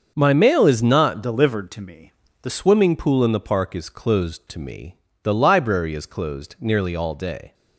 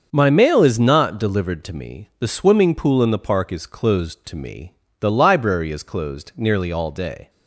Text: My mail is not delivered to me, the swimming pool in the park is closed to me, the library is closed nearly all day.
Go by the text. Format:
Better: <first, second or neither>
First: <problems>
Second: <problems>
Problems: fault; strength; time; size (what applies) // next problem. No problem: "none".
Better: second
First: starts louder than the rest; until 1.1 s; 6.5 dB // changes voice from "delivered" to "the"; from 1.2 to 2.5 s; 1.3 s long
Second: starts louder than the rest; until 1.1 s; 6.5 dB